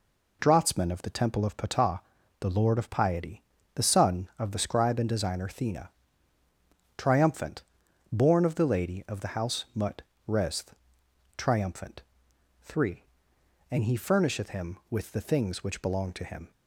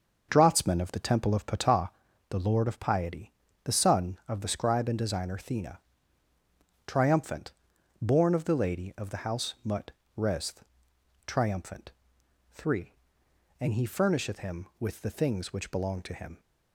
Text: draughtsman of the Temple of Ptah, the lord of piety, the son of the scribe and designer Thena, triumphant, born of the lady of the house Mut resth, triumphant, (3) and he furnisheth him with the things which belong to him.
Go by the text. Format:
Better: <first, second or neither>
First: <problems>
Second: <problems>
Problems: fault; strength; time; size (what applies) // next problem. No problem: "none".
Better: first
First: pauses between "Mut" and "resth"; slight; at 10.0 s; 0.26 s long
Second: starts louder than the rest; until 2.0 s; 6.5 dB // pauses between "Mut" and "resth"; slight; at 9.8 s; 0.26 s long